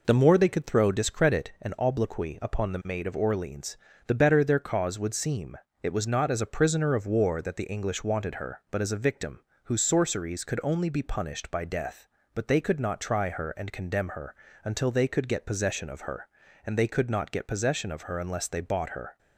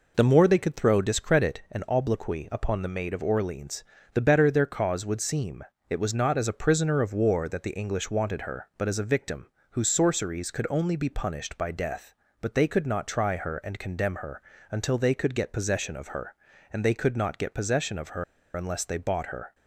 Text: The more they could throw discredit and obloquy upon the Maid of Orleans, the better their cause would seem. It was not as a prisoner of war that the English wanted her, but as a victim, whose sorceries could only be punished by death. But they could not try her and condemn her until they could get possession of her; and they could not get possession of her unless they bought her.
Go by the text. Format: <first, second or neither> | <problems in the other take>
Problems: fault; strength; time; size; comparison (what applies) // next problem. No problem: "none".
first | pauses between "her" and "until"; slight; at 14.4 s; 0.30 s long; slight in the first // pauses between "her" and "unless"; slight; at 18.2 s; 0.30 s long